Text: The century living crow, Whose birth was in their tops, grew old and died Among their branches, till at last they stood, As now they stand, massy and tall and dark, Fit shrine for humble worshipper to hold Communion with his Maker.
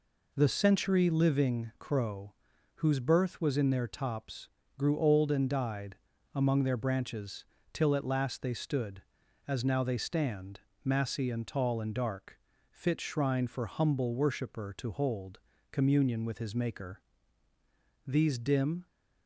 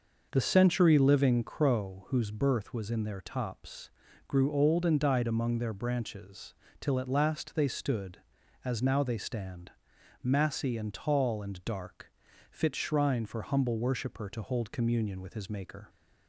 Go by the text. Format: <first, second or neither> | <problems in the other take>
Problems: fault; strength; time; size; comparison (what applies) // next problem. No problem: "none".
second | pauses between "died" and "Among"; at 5.9 s; 0.38 s long // pauses between "hold" and "Communion"; slight; at 15.3 s; 0.32 s long // goes on to say "These dim"; noticeable; from 18.0 s on; 0.80 s long